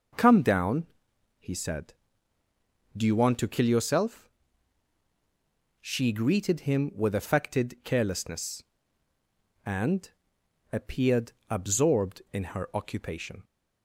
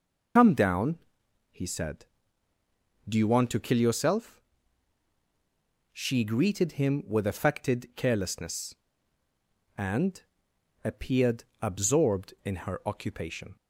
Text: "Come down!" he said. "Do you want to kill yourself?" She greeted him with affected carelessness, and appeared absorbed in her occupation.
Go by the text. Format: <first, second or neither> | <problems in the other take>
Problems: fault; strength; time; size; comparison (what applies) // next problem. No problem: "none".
first | loses the start of "Come"; at 0.3 s; 110 ms // pauses between "and" and "appeared"; noticeable; at 10.2 s; 0.62 s long; noticeable in the first // pauses between "appeared" and "absorbed"; slight; at 11.4 s; 0.18 s long; slight in the first